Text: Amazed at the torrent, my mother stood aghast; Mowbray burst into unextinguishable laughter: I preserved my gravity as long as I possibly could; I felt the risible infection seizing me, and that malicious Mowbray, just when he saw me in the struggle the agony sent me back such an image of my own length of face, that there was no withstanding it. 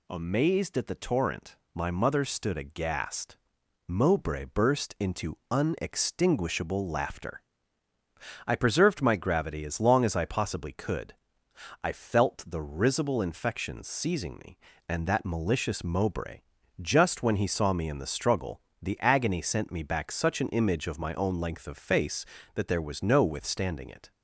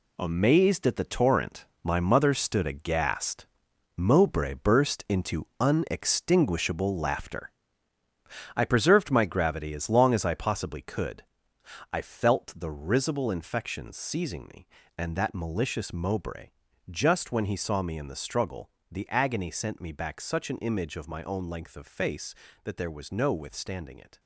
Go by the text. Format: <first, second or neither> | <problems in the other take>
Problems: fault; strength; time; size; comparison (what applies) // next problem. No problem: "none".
first | gets quieter; strong; throughout; 8.5 dB // pauses between "struggle" and "the"; slight; at 18.6 s; 0.22 s long; slight in the first